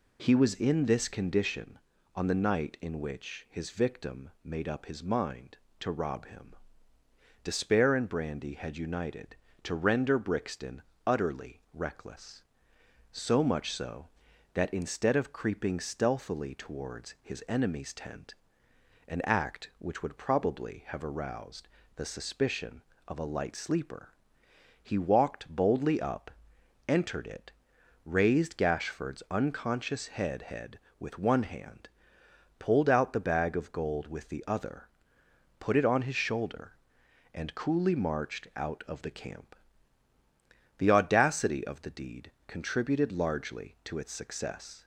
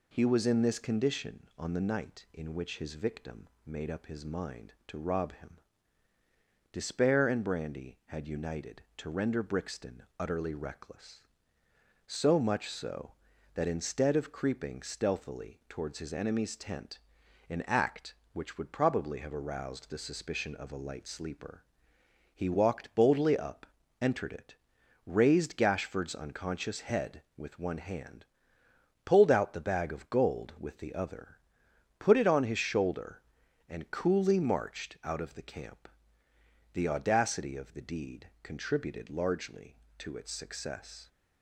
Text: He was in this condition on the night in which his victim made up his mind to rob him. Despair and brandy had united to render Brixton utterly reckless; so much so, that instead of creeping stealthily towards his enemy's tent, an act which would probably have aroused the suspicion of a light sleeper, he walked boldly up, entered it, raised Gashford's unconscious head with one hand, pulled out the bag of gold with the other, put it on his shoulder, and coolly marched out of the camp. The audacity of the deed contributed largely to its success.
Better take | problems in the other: second | pauses between "victim" and "made"; slight; at 4.2 s; 0.16 s long; slight in the second // pauses between "Brixton" and "utterly"; slight; at 10.8 s; 0.24 s long; slight in the second // pauses between "aroused" and "the"; slight; at 21.6 s; 0.28 s long // says "head" twice; at 30.4 s // pauses between "deed" and "contributed"; slight; at 42.3 s; 0.16 s long; slight in the second

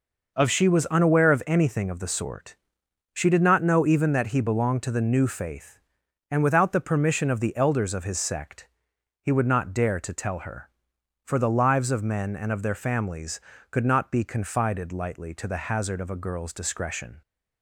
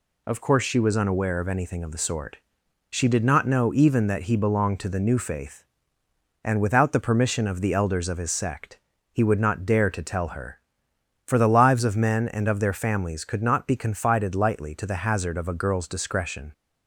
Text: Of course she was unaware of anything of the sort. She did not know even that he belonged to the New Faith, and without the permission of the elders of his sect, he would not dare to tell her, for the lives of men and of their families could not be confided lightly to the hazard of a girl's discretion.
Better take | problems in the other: second | skips "course"; at 0.4 s

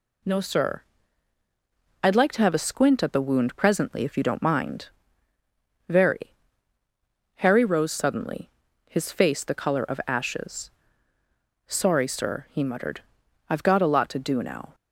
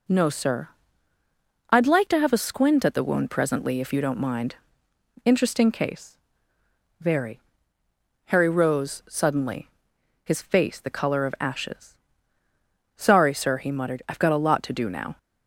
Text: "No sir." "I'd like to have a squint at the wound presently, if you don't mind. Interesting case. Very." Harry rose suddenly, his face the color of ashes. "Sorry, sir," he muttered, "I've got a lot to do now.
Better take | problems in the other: second | skips "Interesting case"; at 5.3 s

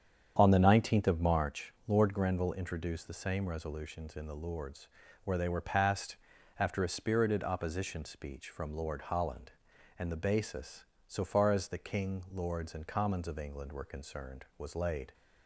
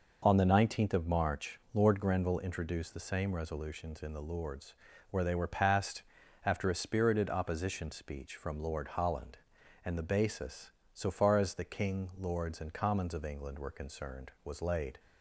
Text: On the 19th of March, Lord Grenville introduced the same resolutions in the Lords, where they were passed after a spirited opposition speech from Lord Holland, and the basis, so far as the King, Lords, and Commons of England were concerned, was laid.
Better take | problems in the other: second | starts louder than the rest; strong; until 1.5 s; 8 dB // pauses between "passed" and "after"; at 6.1 s; 0.44 s long; also in the second

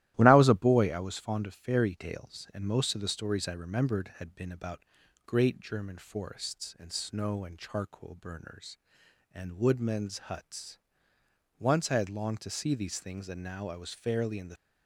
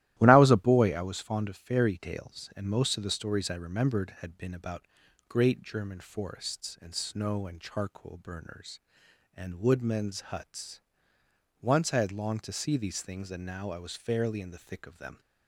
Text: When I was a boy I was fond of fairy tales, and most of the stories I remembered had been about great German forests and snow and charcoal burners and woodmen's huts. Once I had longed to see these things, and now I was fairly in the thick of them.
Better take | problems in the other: second | starts louder than the rest; strong; until 1.1 s; 14.5 dB; strong in the second // pauses between "about" and "great"; noticeable; at 4.7 s; 0.46 s long; noticeable in the second // stops before "thick of them"; at 14.5 s

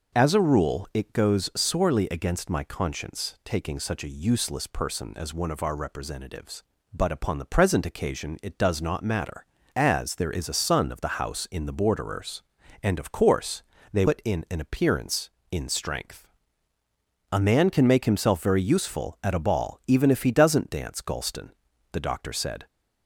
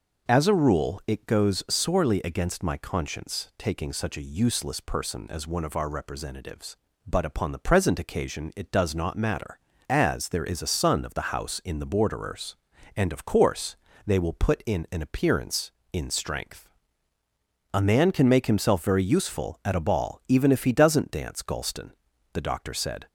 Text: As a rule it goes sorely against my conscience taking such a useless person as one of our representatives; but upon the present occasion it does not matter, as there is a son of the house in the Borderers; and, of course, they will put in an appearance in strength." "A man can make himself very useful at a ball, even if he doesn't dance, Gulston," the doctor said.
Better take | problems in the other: second | skips "will"; at 14.0 s

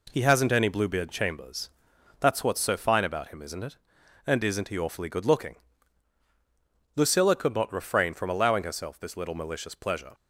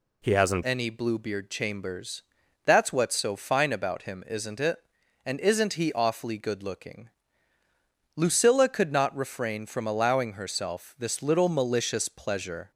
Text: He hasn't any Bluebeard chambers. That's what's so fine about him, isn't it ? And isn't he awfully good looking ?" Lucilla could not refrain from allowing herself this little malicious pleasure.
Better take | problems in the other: first | changes voice at "any"; from 0.6 s on; 12.1 s long

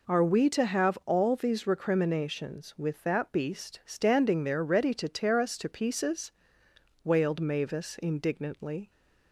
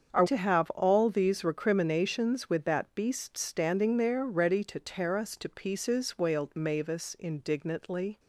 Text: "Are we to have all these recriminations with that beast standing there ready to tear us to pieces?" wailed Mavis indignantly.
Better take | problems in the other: first | starts louder than the rest; strong; until 1.1 s; 7.5 dB // skips "we"; at 0.2 s

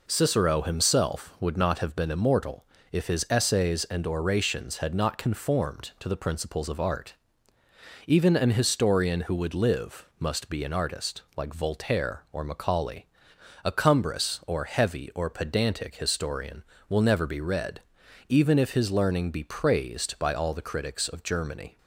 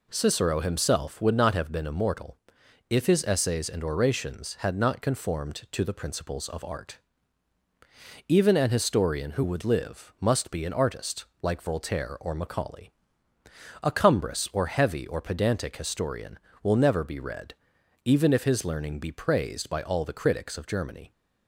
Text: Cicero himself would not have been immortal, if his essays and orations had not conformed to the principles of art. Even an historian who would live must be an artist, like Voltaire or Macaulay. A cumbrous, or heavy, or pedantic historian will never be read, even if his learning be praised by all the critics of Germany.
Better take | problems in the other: neither | none

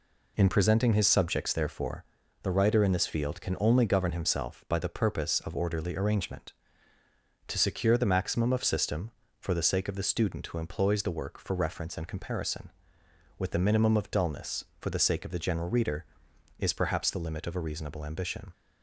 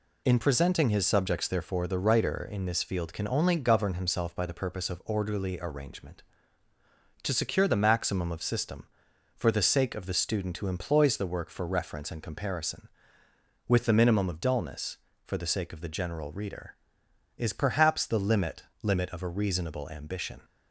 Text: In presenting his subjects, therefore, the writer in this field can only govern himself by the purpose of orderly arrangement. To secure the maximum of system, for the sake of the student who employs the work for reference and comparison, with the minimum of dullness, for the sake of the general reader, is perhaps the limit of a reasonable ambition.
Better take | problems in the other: first | says "limit" twice; at 18.8 s

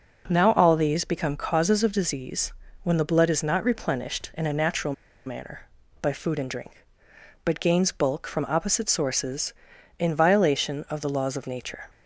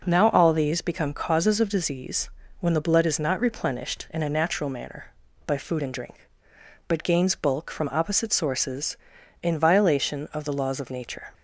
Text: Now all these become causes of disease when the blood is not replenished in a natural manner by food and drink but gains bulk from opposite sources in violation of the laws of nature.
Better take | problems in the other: second | pauses between "disease" and "when"; slight; at 2.5 s; 0.30 s long; slight in the second // pauses between "natural" and "manner"; slight; at 4.9 s; 0.33 s long

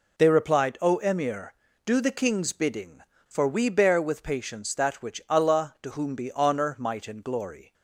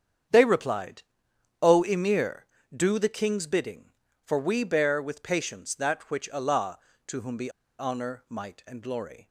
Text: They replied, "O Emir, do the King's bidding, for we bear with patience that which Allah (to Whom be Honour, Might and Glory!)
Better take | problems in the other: first | starts louder than the rest; strong; until 1.8 s; 8 dB // pauses between "be" and "Honour"; slight; at 7.4 s; 0.29 s long

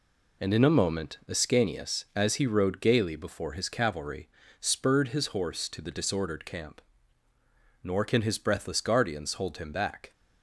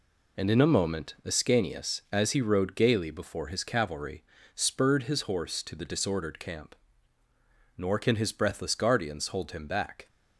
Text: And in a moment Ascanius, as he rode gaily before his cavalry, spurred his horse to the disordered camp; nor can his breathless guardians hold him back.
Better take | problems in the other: neither | none

